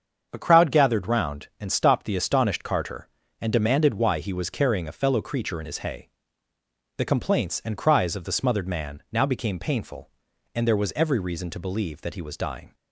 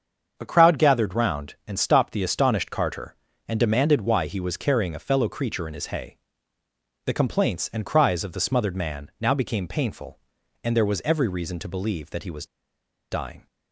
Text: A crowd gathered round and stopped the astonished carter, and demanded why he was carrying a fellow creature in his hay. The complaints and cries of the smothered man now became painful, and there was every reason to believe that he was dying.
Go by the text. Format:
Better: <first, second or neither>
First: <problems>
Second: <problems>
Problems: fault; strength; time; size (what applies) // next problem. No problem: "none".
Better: first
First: starts louder than the rest; until 1.3 s; 7 dB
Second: starts louder than the rest; until 1.3 s; 7 dB // pauses between "was" and "dying"; noticeable; at 12.4 s; 0.66 s long